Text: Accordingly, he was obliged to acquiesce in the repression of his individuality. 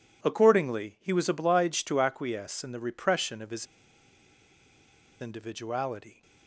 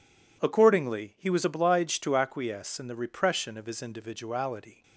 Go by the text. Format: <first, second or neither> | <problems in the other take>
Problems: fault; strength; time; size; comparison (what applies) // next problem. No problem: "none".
second | pauses between "his" and "individuality"; strong; at 3.6 s; 1.5 s long